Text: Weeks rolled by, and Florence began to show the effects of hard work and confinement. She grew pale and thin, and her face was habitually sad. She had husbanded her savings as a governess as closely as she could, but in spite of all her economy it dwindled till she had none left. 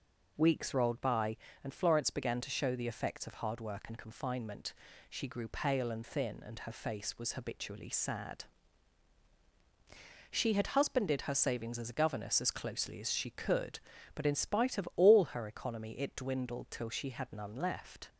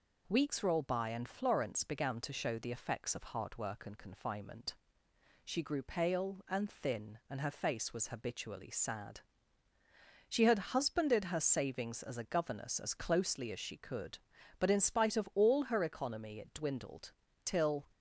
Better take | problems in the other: first | pauses between "dwindled" and "till"; slight; at 17.1 s; 0.32 s long // stops before "she had none left"; at 17.9 s

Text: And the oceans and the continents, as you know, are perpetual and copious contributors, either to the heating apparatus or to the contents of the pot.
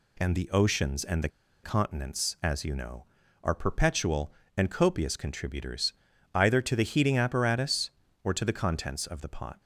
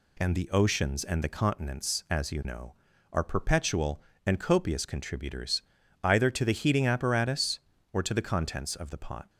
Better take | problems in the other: second | pauses between "the" and "continents"; slight; at 1.2 s; 0.35 s long

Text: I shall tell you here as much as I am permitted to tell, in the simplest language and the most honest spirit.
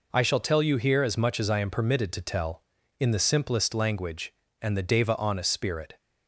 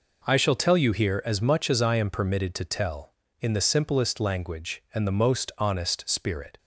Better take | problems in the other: second | says "deva" for "most"; at 4.8 s

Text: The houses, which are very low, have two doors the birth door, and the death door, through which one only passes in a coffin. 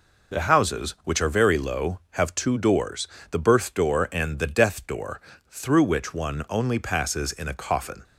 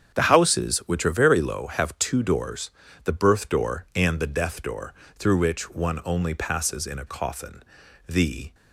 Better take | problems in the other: first | starts louder than the rest; strong; until 1.2 s; 8 dB // pauses between "doors" and "the"; slight; at 2.7 s; 0.34 s long; slight in the first // goes on to say "The"; slight; from 8.0 s on; 0.48 s long

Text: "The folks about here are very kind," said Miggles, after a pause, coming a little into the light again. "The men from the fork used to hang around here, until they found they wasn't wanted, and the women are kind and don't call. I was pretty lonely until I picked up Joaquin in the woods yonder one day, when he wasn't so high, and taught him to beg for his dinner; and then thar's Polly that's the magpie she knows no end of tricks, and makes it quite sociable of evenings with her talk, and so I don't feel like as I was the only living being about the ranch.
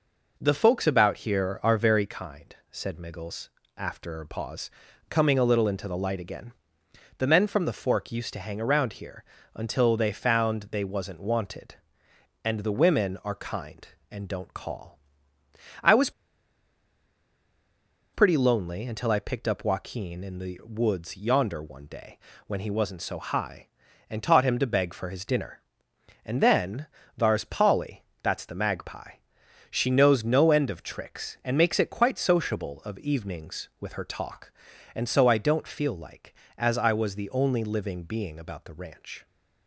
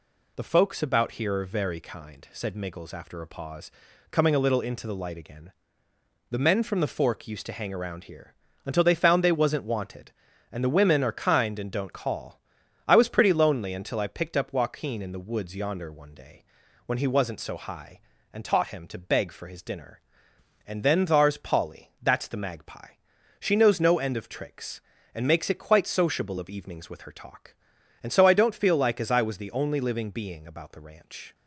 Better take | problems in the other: second | pauses between "was" and "pretty"; strong; at 16.0 s; 2.0 s long // pauses between "then" and "thar's"; slight; at 26.8 s; 0.32 s long // pauses between "Polly" and "that's"; slight; at 28.0 s; 0.16 s long // pauses between "magpie" and "she"; noticeable; at 29.1 s; 0.56 s long; also in the second

